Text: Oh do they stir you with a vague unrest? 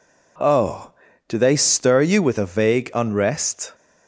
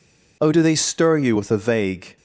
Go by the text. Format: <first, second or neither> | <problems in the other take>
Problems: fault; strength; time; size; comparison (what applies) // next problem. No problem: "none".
first | stops before "unrest"; at 2.1 s